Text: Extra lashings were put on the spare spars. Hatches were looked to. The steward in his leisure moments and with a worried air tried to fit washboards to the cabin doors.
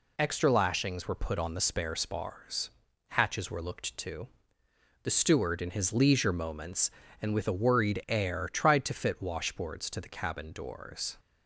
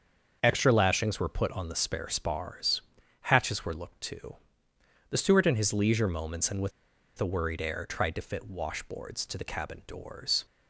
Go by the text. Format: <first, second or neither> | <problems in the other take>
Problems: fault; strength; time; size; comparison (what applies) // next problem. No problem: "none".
first | starts louder than the rest; until 1.4 s; 6.5 dB // pauses between "with" and "a"; noticeable; at 6.7 s; 0.47 s long